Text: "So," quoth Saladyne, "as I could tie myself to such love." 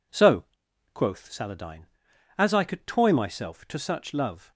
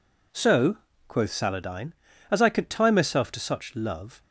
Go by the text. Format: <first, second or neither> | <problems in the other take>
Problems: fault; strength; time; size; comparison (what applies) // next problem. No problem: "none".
second | says "toy" for "tie"; at 2.8 s